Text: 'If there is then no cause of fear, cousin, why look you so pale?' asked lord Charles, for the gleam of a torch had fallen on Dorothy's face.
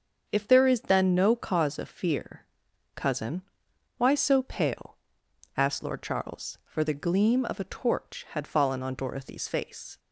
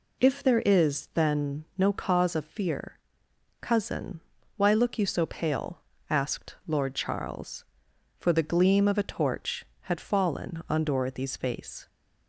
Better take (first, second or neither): second